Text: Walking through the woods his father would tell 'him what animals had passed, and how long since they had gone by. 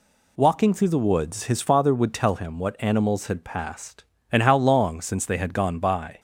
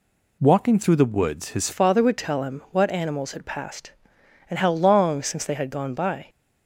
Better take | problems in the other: first | changes voice at "father"; from 1.7 s on; 4.5 s long

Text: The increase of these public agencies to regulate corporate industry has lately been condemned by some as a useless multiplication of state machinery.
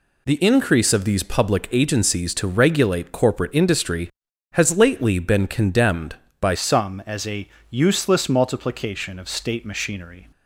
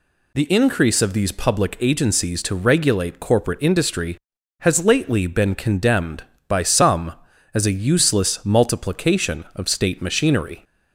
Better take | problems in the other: second | changes voice at "some"; from 6.5 s on; 3.8 s long // pauses between "a" and "useless"; slight; at 7.4 s; 0.20 s long

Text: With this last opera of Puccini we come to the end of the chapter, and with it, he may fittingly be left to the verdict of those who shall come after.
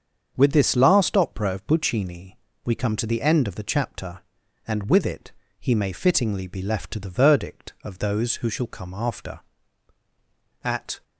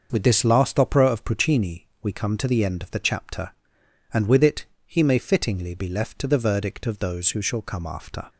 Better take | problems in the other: second | starts louder than the rest; strong; until 1.3 s; 7 dB; also in the second // pauses between "Puccini" and "we"; slight; at 2.3 s; 0.28 s long; slight in the second // goes on to say "At"; slight; from 10.6 s on; 0.40 s long

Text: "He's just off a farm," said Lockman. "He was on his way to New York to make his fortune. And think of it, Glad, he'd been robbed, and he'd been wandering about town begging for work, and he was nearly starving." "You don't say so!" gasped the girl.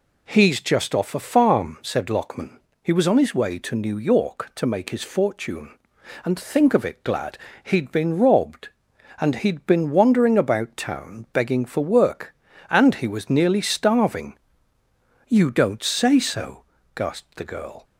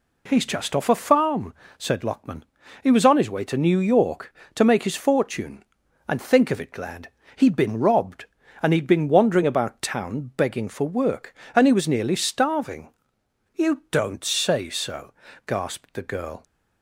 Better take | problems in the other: neither | none

